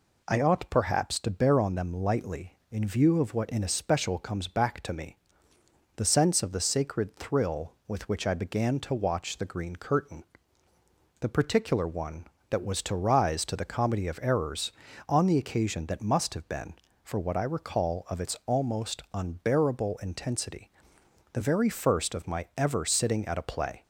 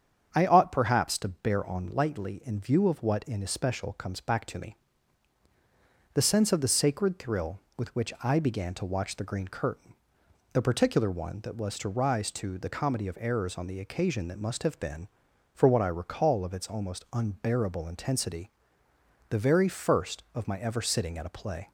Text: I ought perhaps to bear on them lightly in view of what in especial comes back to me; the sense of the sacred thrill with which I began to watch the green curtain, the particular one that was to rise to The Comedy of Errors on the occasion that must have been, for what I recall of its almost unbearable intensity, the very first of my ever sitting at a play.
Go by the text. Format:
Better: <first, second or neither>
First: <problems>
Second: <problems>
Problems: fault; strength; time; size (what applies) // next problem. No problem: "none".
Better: first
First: none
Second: starts louder than the rest; strong; until 1.3 s; 8 dB // skips "them"; at 1.8 s